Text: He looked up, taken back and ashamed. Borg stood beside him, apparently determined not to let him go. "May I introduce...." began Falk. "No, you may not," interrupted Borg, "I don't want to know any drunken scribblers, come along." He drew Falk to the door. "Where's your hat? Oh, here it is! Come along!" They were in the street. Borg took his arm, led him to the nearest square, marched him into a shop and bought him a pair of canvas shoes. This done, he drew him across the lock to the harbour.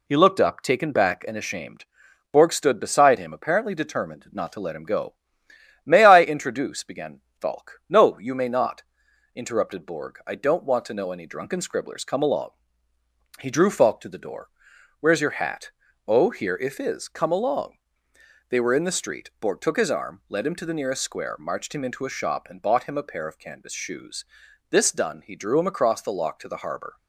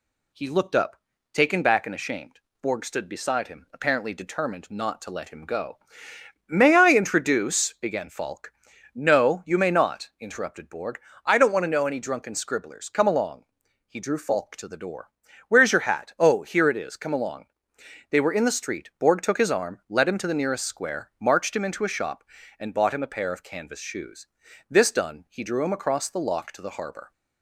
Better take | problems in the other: second | pauses between "began" and "Falk"; slight; at 7.1 s; 0.22 s long // says "if" for "it"; at 16.5 s

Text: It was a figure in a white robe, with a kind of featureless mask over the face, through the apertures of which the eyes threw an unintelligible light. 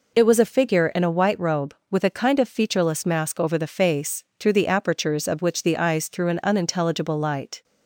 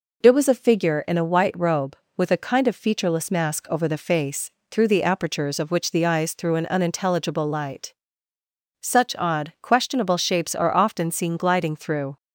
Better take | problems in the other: first | goes on to say "Such odd questionable shapes are often seen gliding through"; strong; from 8.8 s on; 3.3 s long

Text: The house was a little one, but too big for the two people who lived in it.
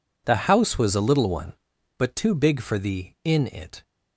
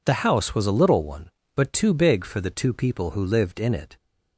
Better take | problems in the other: second | skips "two people who lived"; at 3.1 s

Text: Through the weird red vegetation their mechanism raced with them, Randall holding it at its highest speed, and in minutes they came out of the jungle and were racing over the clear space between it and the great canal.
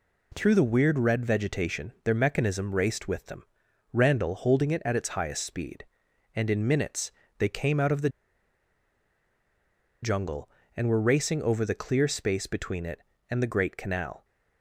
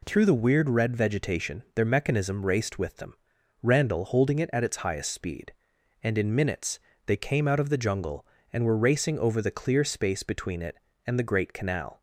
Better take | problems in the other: second | pauses between "minutes" and "they"; slight; at 7.1 s; 0.26 s long; slight in the second // pauses between "the" and "jungle"; strong; at 8.0 s; 1.9 s long

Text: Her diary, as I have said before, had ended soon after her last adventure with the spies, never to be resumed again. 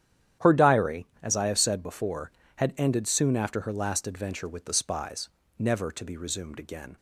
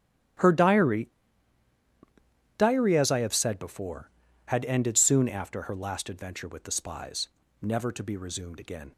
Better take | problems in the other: first | starts louder than the rest; strong; until 2.8 s; 12 dB; strong in the first // says "diary" twice; at 2.5 s

